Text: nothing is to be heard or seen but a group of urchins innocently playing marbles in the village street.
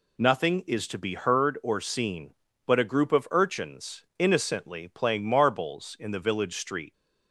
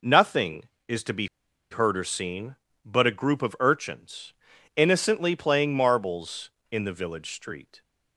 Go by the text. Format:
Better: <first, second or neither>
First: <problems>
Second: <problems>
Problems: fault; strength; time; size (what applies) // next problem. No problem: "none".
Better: first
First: none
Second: pauses between "be" and "heard"; at 1.2 s; 0.44 s long // pauses between "urchins" and "innocently"; at 4.3 s; 0.42 s long